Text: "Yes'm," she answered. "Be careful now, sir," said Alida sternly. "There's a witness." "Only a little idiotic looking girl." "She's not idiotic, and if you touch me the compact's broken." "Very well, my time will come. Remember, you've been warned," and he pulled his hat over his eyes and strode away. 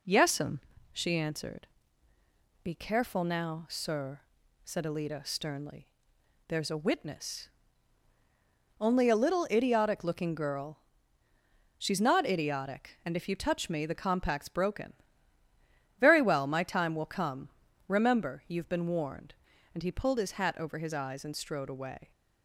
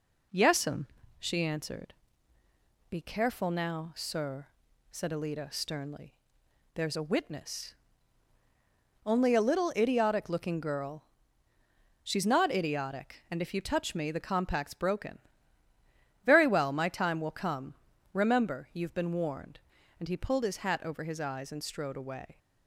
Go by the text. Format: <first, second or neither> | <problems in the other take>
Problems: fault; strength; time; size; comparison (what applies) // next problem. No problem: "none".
neither | none